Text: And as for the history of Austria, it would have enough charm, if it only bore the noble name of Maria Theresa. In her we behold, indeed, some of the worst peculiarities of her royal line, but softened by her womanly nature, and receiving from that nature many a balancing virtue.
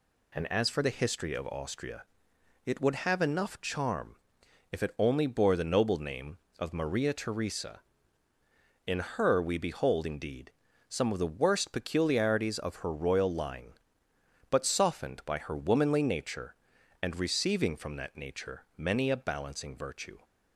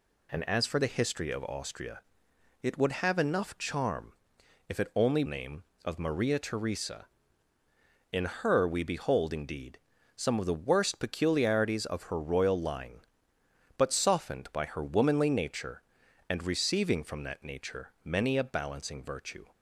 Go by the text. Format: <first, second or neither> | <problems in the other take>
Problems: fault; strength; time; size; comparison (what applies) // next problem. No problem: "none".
first | skips "bore the noble"; at 5.2 s